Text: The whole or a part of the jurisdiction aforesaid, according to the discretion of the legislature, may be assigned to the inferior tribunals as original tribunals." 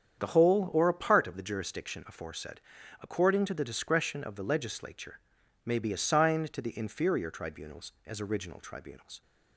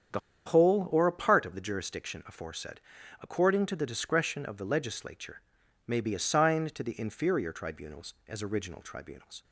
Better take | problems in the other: first | starts louder than the rest; strong; until 1.4 s; 8 dB; strong in the first // pauses between "The" and "whole"; slight; at 0.1 s; 0.26 s long

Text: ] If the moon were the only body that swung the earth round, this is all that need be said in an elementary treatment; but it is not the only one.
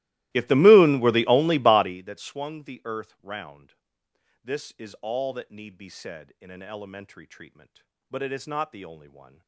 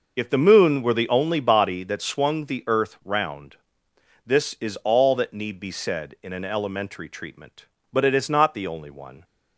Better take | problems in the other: second | starts louder than the rest; strong; until 2.0 s; 17 dB

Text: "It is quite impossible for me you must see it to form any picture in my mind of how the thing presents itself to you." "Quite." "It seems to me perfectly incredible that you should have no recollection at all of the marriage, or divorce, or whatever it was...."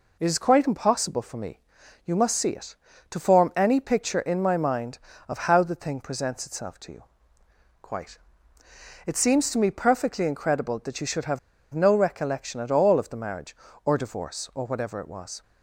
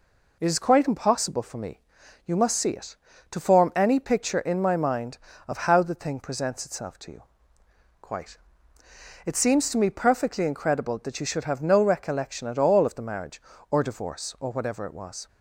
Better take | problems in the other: second | pauses between "me" and "you"; noticeable; at 1.5 s; 0.46 s long; noticeable in the second // pauses between "have" and "no"; slight; at 11.3 s; 0.34 s long

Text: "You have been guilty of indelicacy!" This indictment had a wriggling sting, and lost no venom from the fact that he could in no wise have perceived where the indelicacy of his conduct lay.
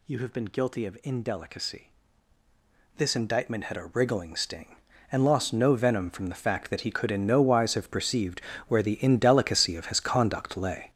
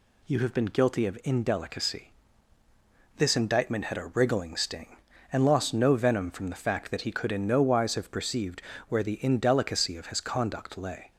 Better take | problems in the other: second | gets louder; strong; throughout; 10 dB // pauses between "perceived" and "where"; slight; at 8.4 s; 0.24 s long; slight in the second

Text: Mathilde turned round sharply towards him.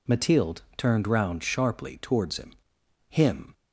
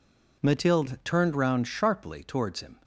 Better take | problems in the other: second | pauses between "Mathilde" and "turned"; slight; at 0.6 s; 0.16 s long // says "him" twice; at 3.0 s

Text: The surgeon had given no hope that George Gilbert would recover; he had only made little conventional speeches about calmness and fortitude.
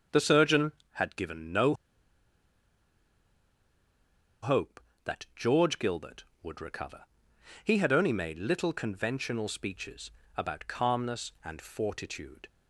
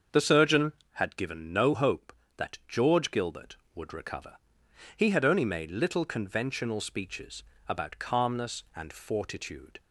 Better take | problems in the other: second | starts louder than the rest; until 1.3 s; 7 dB; also in the second // pauses between "no" and "hope"; strong; at 1.7 s; 2.6 s long // pauses between "speeches" and "about"; slight; at 10.0 s; 0.26 s long; slight in the second

